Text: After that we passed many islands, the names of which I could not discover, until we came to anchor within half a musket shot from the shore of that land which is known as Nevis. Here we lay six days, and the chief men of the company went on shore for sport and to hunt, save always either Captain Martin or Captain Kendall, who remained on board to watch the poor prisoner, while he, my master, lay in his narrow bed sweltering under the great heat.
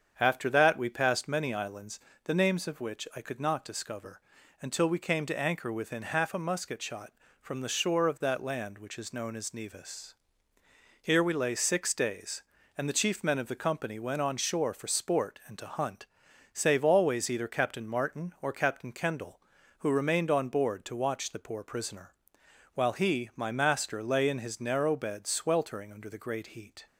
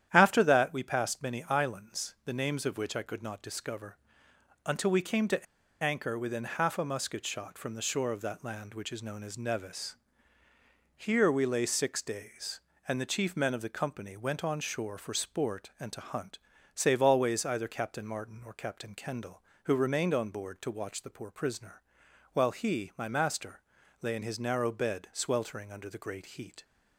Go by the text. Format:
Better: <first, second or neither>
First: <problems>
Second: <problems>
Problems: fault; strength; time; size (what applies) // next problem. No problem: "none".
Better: first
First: starts louder than the rest; strong; until 1.2 s; 8 dB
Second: starts louder than the rest; strong; until 1.1 s; 10.5 dB // pauses between "to" and "anchor"; at 5.4 s; 0.38 s long